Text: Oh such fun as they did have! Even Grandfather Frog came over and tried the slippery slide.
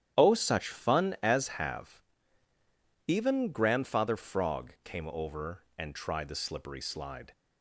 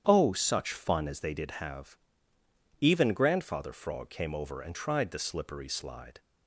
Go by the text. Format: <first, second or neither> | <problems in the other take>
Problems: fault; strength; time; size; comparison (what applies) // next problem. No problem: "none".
second | starts louder than the rest; strong; until 1.2 s; 10 dB; strong in the second // skips "they did"; at 1.5 s